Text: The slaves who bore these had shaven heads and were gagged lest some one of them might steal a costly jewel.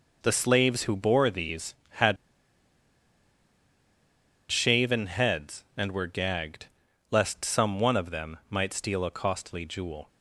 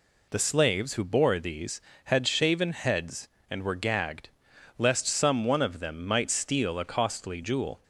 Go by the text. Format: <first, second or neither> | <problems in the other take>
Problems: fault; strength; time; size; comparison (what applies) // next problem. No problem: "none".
second | pauses between "had" and "shaven"; strong; at 2.1 s; 2.3 s long // pauses between "gagged" and "lest"; at 6.6 s; 0.42 s long; noticeable in the second